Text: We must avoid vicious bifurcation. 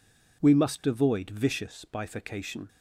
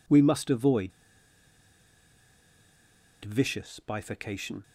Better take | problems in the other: first | pauses between "avoid" and "vicious"; strong; at 0.9 s; 2.3 s long

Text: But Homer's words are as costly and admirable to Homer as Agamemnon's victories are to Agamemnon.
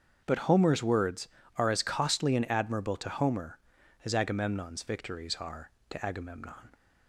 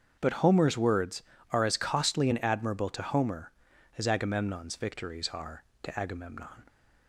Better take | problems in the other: neither | starts louder than the rest; strong; the same in both

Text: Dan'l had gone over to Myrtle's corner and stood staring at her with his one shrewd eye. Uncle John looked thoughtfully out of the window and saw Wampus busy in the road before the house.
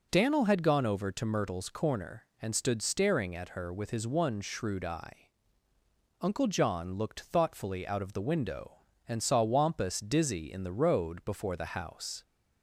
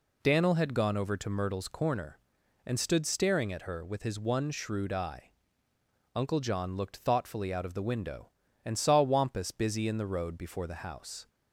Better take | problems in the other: second | says "dizzy" for "busy"; at 9.9 s

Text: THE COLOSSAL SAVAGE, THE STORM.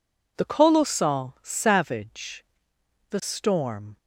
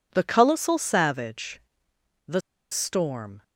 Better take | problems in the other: first | pauses between "THE" and "STORM"; slight; at 2.4 s; 0.31 s long

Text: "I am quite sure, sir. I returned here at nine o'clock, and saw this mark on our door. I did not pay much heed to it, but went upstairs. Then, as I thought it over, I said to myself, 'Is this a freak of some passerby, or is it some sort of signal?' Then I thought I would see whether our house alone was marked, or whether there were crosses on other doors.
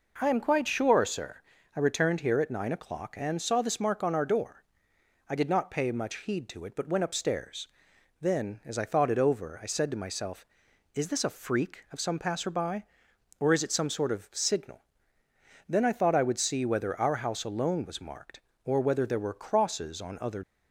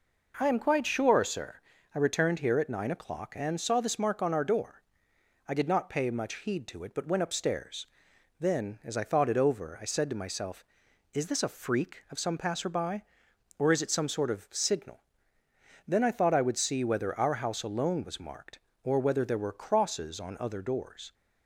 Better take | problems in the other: second | stops before "doors"; at 20.4 s

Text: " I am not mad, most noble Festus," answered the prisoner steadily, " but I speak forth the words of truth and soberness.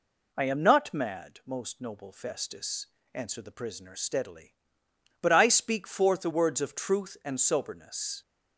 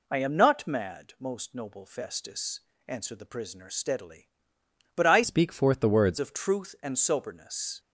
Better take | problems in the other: first | changes voice from "speak" to "words"; from 5.2 to 6.1 s; 0.9 s long

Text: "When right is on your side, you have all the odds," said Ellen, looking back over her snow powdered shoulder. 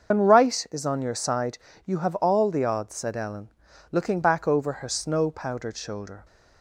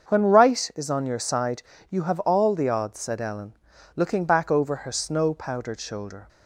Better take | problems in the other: second | loses the start of "When"; at 0.1 s; 70 ms // starts louder than the rest; until 1.1 s; 6.5 dB; also in the second

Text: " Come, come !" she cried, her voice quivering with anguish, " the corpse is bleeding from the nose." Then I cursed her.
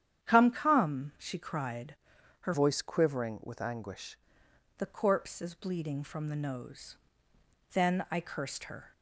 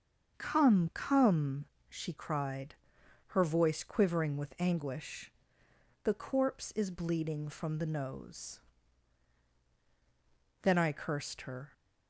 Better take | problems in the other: second | starts louder than the rest; strong; until 1.2 s; 10 dB; also in the second // changes voice from "voice" to "anguish"; from 2.5 to 4.1 s; 1.6 s long

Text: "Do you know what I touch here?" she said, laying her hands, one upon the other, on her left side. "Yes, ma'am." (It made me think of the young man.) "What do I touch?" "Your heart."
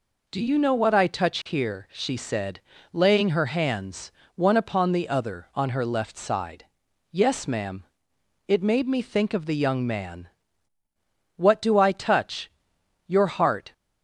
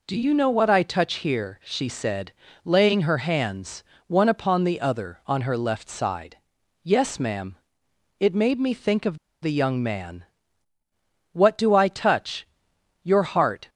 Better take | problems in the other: first | pauses between "of" and "the"; slight; at 9.1 s; 0.25 s long

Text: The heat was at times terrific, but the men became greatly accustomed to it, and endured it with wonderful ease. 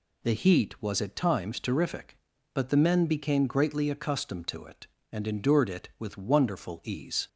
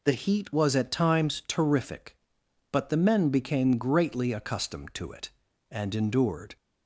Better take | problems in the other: first | stops before "it with wonderful ease"; at 6.5 s

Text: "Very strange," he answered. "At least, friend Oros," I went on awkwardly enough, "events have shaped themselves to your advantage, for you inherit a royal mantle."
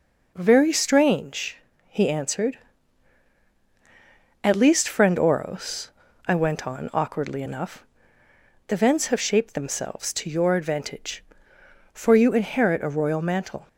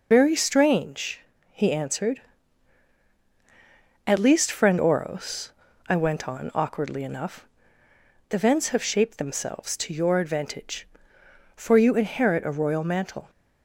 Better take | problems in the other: first | loses the start of "Very"; at 0.1 s; 125 ms

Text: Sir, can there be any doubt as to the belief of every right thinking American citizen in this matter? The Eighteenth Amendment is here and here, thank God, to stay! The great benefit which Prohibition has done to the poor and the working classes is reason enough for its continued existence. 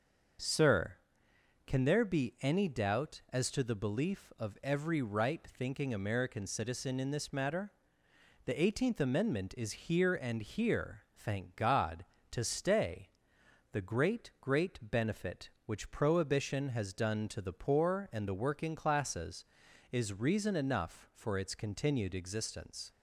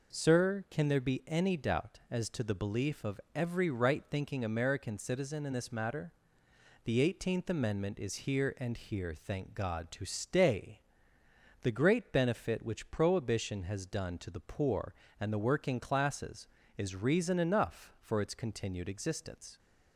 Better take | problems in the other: second | says "great" twice; at 14.4 s

